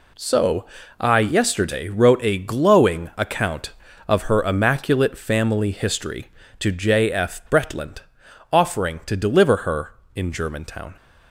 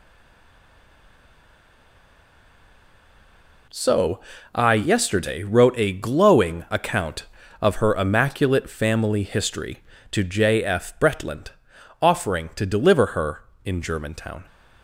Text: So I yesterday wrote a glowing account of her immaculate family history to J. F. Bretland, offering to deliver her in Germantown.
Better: first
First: pauses between "So" and "I"; slight; at 0.6 s; 0.34 s long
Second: stays silent before the first word; strong; until 3.6 s; 3.6 s long // pauses between "So" and "I"; slight; at 4.1 s; 0.34 s long

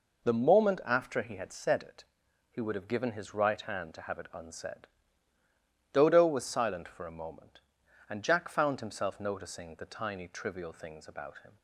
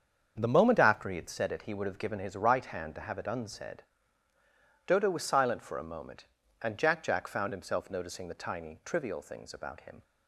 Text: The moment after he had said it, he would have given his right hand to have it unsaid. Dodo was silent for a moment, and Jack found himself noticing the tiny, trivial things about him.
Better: first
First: none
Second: starts louder than the rest; strong; until 1.3 s; 7 dB // says "Jack" twice; at 7.0 s

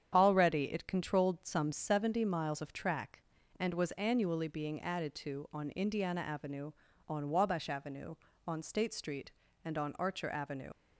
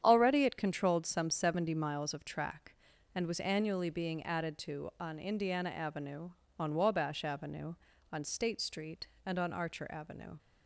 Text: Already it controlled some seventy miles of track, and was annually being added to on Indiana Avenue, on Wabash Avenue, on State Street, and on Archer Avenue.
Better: second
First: starts louder than the rest; strong; until 1.1 s; 8.5 dB // leaves "Avenue" unfinished; at 10.7 s; 75 ms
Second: starts louder than the rest; strong; until 1.0 s; 9 dB

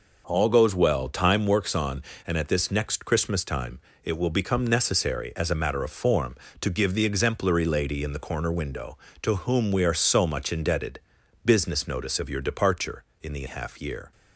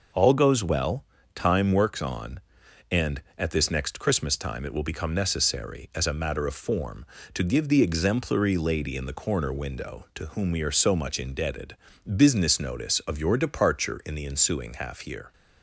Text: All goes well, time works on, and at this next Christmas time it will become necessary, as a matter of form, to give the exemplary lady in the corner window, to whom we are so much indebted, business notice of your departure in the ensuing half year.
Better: second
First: pauses between "time" and "it"; slight; at 3.7 s; 0.24 s long // skips "ensuing"; at 13.4 s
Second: none

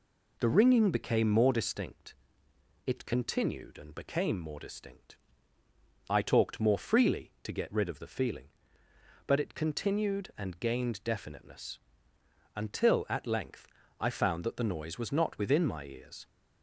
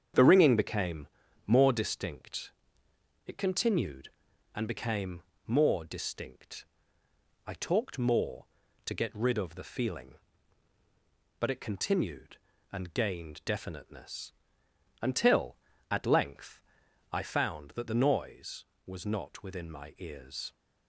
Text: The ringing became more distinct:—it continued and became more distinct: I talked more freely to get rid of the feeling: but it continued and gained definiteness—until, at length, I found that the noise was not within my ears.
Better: first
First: none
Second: starts louder than the rest; strong; until 1.5 s; 8 dB // pauses between "became" and "more"; slight; at 1.0 s; 0.36 s long // pauses between "became" and "more"; slight; at 5.2 s; 0.22 s long // skips "freely"; at 8.6 s

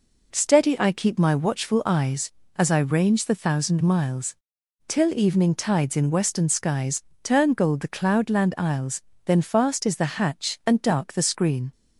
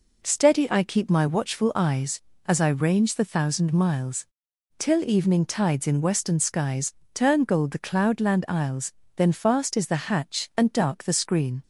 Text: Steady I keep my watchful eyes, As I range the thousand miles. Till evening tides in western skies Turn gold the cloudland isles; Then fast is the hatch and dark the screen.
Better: neither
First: pauses between "skies" and "Turn"; slight; at 7.0 s; 0.22 s long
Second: pauses between "skies" and "Turn"; slight; at 6.9 s; 0.22 s long

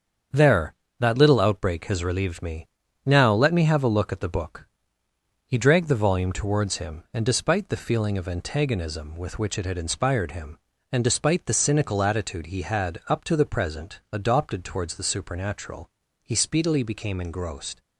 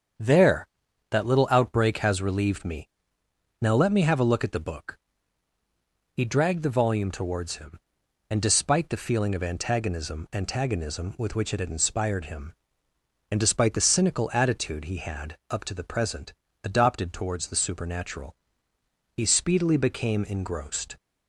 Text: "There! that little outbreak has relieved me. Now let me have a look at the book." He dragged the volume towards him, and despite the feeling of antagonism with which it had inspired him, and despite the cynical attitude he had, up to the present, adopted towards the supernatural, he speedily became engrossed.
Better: first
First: starts louder than the rest; strong; until 1.5 s; 7.5 dB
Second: starts louder than the rest; strong; until 1.6 s; 7.5 dB // says "antagonism" twice; at 10.3 s

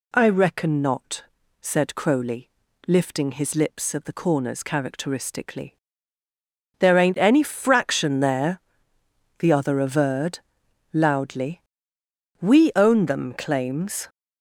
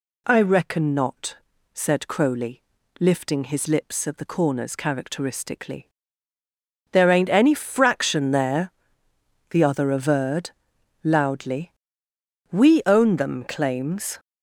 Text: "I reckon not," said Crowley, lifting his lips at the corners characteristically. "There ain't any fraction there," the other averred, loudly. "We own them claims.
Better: neither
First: none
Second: none

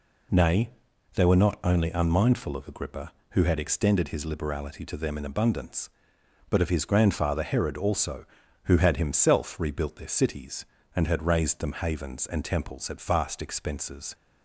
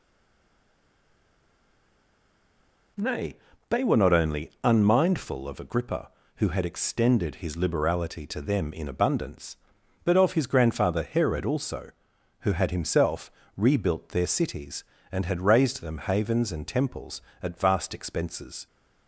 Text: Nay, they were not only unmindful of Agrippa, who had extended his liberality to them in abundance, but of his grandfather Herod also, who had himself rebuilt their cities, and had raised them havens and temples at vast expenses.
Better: first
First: none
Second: stays silent before the first word; strong; until 2.9 s; 2.9 s long // pauses between "himself" and "rebuilt"; slight; at 13.3 s; 0.26 s long

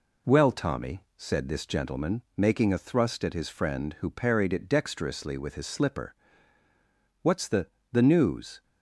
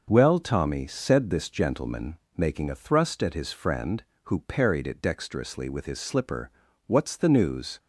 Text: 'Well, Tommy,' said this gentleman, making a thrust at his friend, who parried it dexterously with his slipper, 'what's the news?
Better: second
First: says "the" twice; at 7.9 s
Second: none

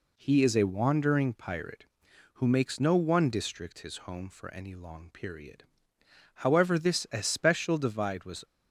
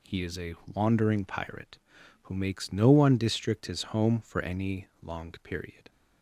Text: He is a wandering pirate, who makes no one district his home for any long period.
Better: second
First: goes on to say "However this especial divide was"; strong; from 6.4 s on; 2.0 s long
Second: none

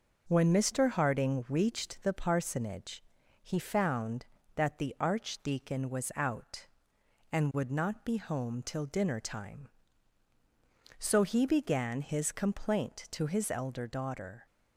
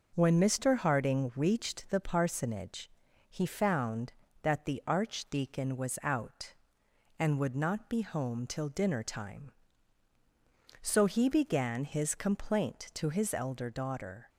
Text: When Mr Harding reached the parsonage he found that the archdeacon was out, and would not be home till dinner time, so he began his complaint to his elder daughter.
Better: neither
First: pauses between "parsonage" and "he"; at 3.0 s; 0.42 s long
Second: pauses between "parsonage" and "he"; at 2.8 s; 0.42 s long

